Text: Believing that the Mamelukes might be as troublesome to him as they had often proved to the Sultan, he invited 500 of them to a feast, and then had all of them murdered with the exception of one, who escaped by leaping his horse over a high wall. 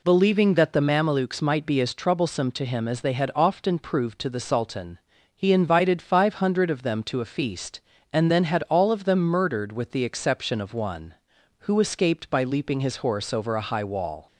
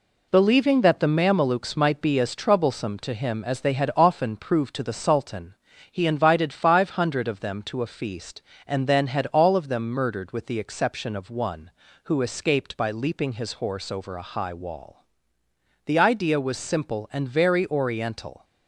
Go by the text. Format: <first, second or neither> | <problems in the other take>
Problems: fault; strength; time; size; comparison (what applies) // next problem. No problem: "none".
first | goes on to say "The idea was simple and very oriental"; strong; from 15.8 s on; 2.5 s long